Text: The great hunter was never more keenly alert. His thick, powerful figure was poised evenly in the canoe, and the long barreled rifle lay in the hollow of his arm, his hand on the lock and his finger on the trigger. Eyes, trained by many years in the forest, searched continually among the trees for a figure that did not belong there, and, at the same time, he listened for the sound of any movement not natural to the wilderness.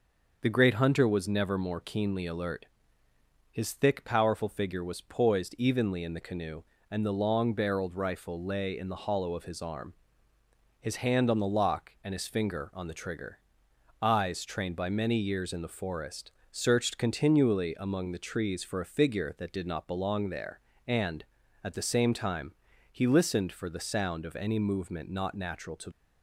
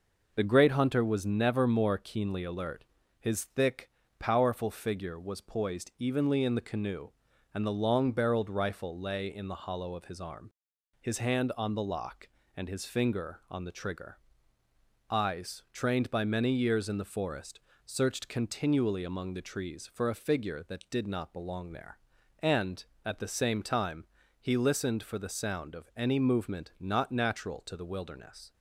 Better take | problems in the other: second | stops before "the wilderness"; at 25.9 s

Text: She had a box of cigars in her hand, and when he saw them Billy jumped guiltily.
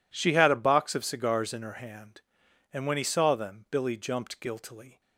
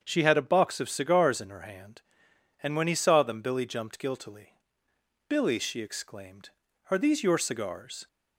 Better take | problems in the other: first | starts louder than the rest; strong; until 1.0 s; 7.5 dB // goes on to say "Billy she exclaimed Are these your cigars"; strong; from 5.2 s on; 2.7 s long

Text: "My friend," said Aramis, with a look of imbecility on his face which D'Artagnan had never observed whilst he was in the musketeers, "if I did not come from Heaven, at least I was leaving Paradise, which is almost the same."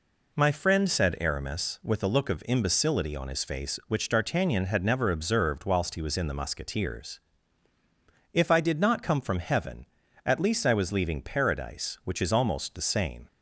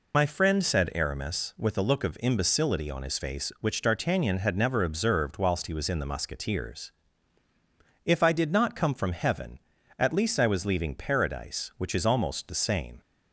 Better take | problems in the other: first | loses the start of "My"; at 0.1 s; 60 ms

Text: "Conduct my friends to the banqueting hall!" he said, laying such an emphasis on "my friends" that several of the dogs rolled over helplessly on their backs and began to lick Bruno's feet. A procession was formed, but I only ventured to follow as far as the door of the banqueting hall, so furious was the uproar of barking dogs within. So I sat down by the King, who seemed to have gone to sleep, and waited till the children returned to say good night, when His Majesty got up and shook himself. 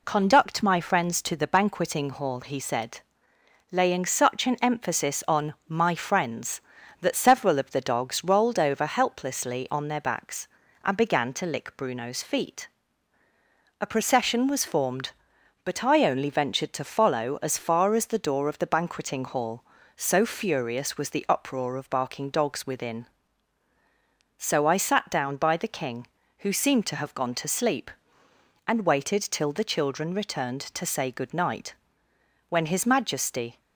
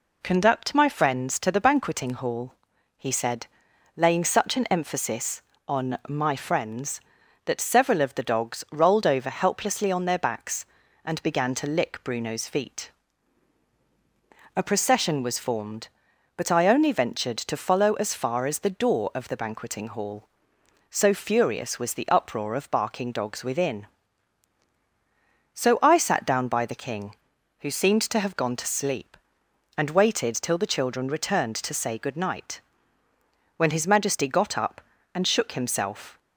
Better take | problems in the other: second | stops before "got up and shook himself"; at 33.5 s

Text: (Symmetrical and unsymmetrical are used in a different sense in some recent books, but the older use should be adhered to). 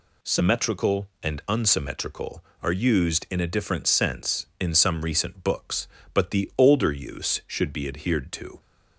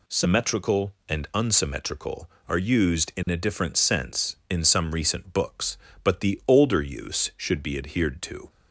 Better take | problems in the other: neither | none

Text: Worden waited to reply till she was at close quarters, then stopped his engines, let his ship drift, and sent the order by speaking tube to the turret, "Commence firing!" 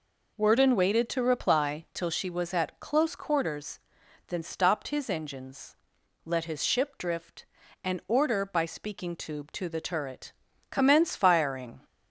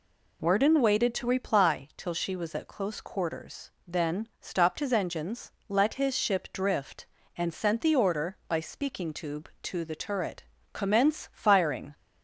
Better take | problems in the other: second | skips "sent the"; at 8.0 s

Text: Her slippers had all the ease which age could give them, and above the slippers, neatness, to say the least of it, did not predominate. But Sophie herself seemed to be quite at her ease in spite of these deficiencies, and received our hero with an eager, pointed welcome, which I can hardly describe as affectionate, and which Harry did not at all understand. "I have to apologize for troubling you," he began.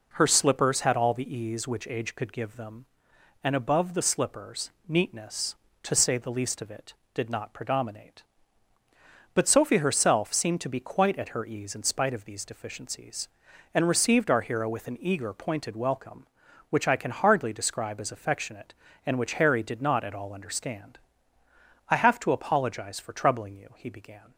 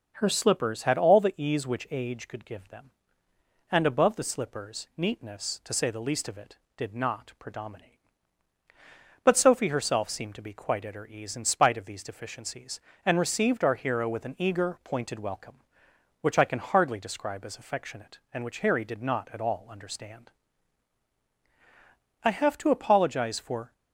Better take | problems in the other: first | starts louder than the rest; until 1.1 s; 6.5 dB // stops before "troubling you he began"; at 23.7 s

